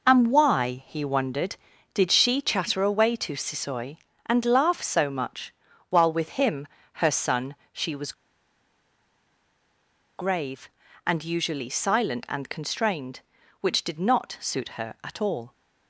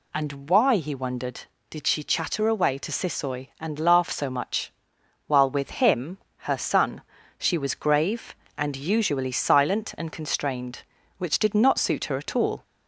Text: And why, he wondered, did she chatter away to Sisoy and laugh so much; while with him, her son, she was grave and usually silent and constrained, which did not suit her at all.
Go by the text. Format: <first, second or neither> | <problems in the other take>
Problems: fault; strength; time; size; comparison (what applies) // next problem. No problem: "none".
second | pauses between "was" and "grave"; strong; at 8.1 s; 2.0 s long